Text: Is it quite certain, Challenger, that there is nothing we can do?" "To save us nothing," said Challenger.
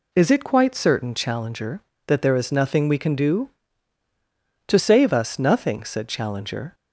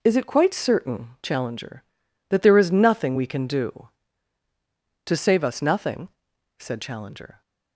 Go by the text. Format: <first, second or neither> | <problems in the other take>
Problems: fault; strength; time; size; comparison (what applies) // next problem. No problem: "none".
neither | none